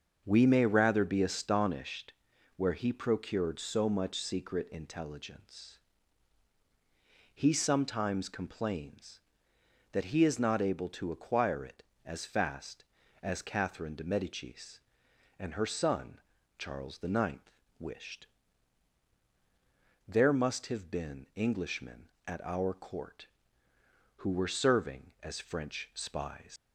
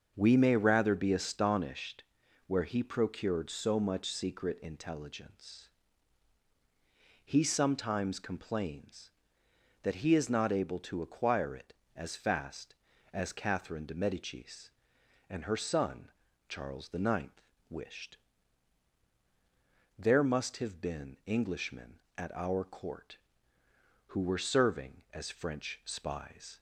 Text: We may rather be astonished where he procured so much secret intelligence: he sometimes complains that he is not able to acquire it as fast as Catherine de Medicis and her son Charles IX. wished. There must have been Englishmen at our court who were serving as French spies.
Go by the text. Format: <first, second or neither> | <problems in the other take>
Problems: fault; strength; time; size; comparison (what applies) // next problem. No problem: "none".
second | starts louder than the rest; until 1.2 s; 6.5 dB; also in the second // pauses between "astonished" and "where"; at 2.1 s; 0.44 s long; also in the second // pauses between "son" and "Charles"; at 16.1 s; 0.40 s long; also in the second // leaves "spies" unfinished; at 26.5 s; 125 ms